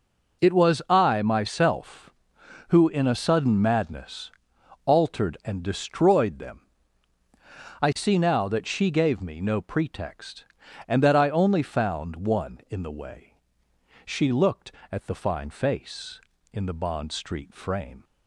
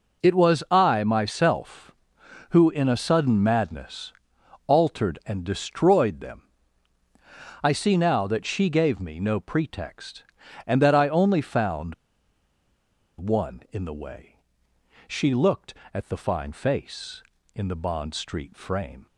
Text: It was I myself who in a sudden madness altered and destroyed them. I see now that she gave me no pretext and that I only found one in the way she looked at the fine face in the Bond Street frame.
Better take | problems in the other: first | pauses between "madness" and "altered"; noticeable; at 4.1 s; 0.54 s long; noticeable in the first // pauses between "found" and "one"; at 11.9 s; 1.2 s long // pauses between "way" and "she"; noticeable; at 14.3 s; 0.70 s long; noticeable in the first

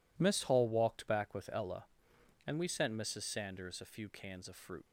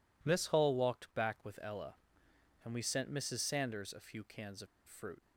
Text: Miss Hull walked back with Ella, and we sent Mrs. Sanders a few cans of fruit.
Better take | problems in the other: first | pauses between "of" and "fruit"; slight; at 4.6 s; 0.21 s long

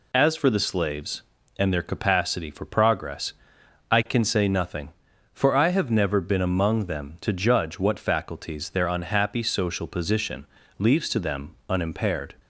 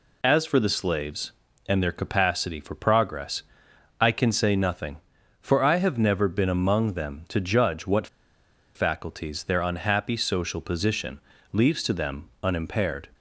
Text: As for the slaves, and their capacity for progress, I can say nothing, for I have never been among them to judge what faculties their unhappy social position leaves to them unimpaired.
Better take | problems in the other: first | pauses between "what" and "faculties"; noticeable; at 8.0 s; 0.68 s long // pauses between "position" and "leaves"; slight; at 11.2 s; 0.32 s long; slight in the first

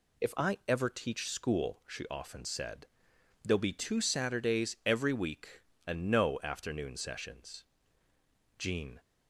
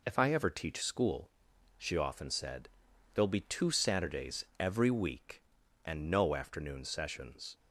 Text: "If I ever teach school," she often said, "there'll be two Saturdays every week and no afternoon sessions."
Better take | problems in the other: second | goes on to say "Jean"; slight; from 8.5 s on; 0.42 s long

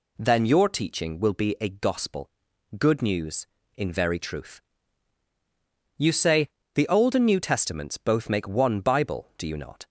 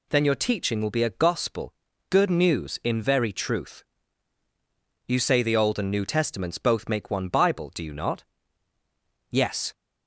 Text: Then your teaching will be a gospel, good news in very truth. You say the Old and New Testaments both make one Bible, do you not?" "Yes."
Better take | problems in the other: second | pauses between "say" and "the"; slight; at 6.4 s; 0.26 s long // stops before "Yes"; at 9.8 s

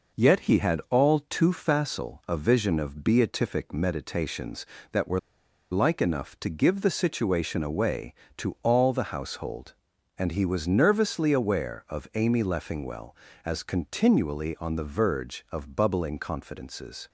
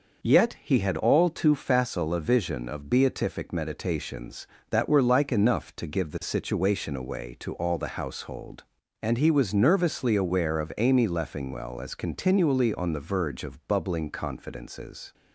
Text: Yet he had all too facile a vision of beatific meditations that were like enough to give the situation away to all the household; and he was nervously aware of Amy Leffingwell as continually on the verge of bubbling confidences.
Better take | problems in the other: second | pauses between "were" and "like"; noticeable; at 5.1 s; 0.52 s long

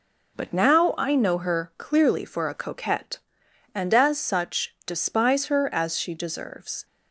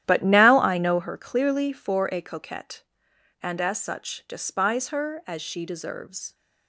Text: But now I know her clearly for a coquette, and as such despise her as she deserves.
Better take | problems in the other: first | starts louder than the rest; strong; until 1.1 s; 12 dB

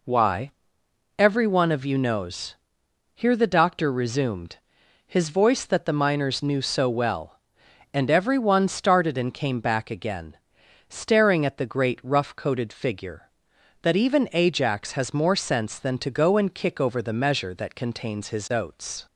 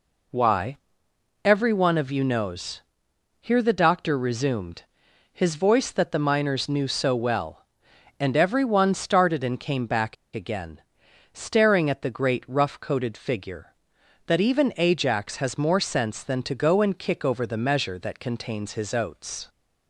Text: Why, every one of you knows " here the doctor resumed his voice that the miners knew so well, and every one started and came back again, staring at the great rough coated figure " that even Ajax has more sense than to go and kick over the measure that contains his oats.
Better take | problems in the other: first | pauses between "resumed" and "his"; noticeable; at 4.8 s; 0.50 s long; noticeable in the first // pauses between "back" and "again"; slight; at 10.1 s; 0.19 s long

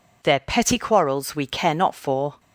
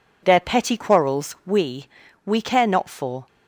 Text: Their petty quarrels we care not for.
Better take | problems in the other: first | says "we" twice; at 2.2 s

